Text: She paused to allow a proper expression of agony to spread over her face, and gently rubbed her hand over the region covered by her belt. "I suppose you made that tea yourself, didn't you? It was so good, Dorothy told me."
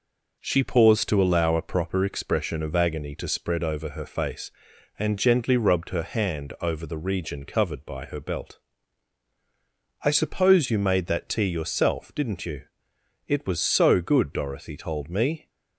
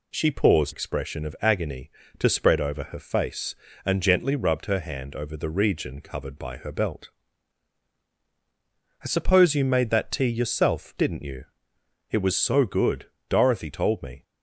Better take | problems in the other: first | skips "to allow a proper"; at 0.7 s

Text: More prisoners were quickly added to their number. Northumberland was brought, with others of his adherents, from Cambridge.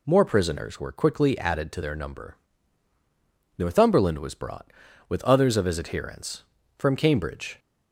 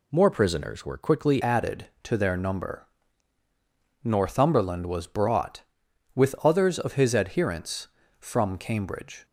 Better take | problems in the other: first | changes voice at "added"; from 1.4 s on; 7.8 s long

